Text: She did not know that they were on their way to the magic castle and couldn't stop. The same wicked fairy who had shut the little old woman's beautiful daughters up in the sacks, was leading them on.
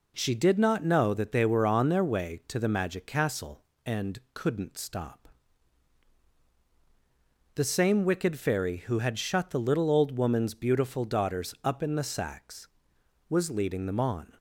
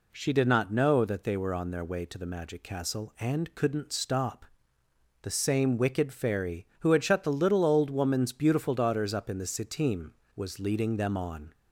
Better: first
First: none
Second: says "sitim" for "sacks"; at 9.4 s

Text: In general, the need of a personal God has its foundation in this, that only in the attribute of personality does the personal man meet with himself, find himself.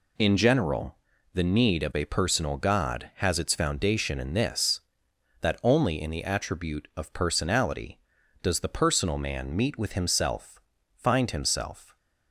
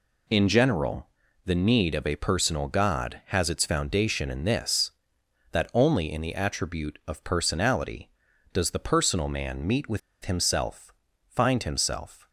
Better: first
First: none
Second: pauses between "with" and "himself"; slight; at 9.9 s; 0.24 s long

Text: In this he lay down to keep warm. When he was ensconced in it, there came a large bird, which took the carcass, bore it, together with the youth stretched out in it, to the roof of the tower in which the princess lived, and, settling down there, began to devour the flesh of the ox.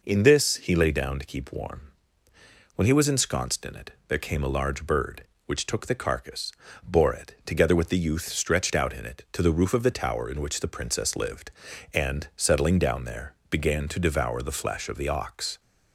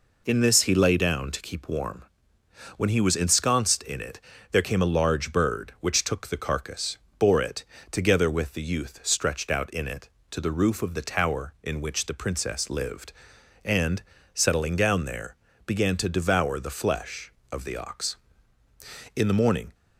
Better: first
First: none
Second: goes on to say "In the morning"; from 19.1 s on; 0.60 s long

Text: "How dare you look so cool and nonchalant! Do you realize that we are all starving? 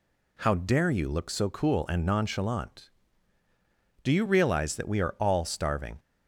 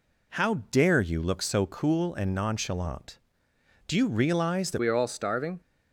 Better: first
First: none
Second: changes voice at "we"; from 4.7 s on; 0.9 s long

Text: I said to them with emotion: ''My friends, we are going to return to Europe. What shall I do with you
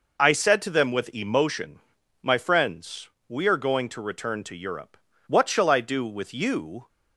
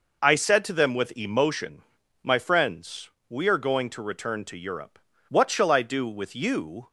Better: neither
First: none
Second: none

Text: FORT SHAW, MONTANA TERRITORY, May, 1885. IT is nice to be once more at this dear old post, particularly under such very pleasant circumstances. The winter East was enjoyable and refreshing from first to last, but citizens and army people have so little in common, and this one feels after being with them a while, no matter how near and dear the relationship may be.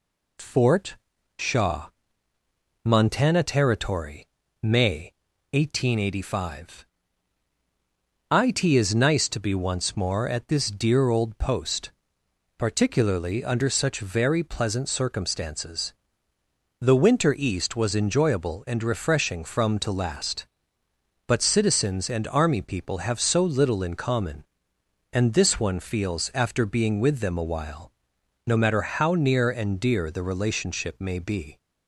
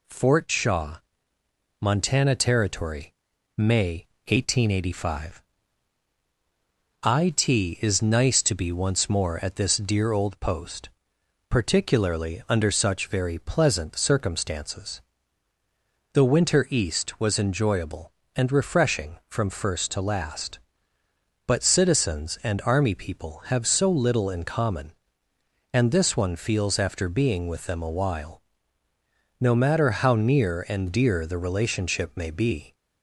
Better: second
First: pauses between "FORT" and "SHAW"; at 0.9 s; 0.42 s long // skips "first"; at 19.7 s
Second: none

